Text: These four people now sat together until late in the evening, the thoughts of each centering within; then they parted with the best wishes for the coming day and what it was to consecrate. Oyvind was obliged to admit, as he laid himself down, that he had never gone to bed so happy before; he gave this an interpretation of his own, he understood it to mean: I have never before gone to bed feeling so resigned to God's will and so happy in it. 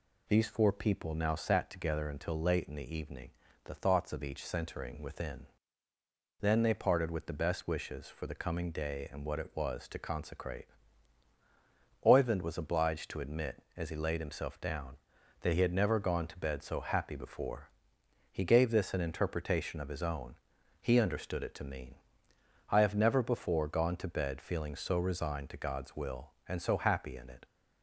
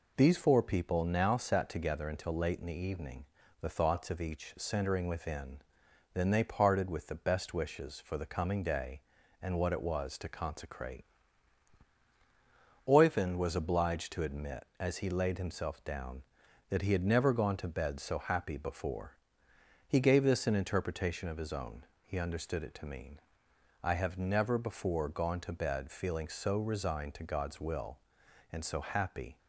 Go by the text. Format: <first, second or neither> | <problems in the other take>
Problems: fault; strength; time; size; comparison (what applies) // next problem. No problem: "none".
first | stops before "in it"; at 29.3 s